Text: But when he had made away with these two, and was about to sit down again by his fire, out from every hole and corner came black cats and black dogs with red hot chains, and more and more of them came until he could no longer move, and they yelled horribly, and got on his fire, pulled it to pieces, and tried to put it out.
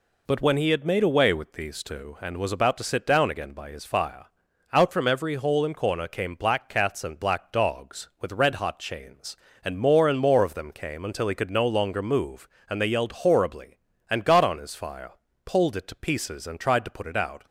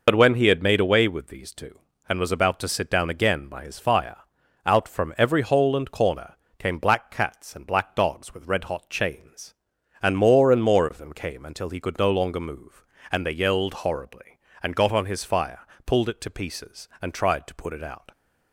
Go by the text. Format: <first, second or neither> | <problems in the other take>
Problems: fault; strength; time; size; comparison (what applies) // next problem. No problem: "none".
first | loses the start of "But"; at 0.0 s; 55 ms // pauses between "corner" and "came"; slight; at 6.3 s; 0.24 s long